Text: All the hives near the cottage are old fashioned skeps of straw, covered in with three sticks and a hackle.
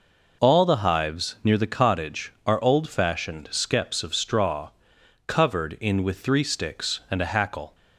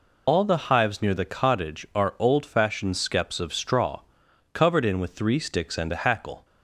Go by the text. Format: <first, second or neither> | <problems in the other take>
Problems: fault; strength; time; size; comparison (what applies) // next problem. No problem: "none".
first | loses the start of "All"; at 0.2 s; 70 ms